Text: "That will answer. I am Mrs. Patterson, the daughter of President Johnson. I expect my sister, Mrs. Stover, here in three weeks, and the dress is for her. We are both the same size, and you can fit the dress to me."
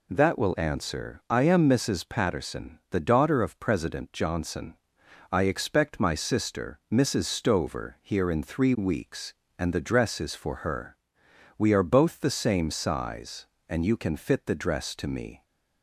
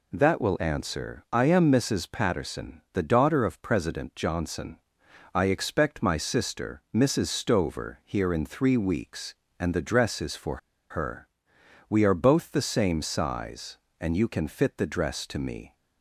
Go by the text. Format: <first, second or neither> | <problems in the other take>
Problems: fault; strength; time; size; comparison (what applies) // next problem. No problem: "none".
first | pauses between "for" and "her"; slight; at 10.5 s; 0.32 s long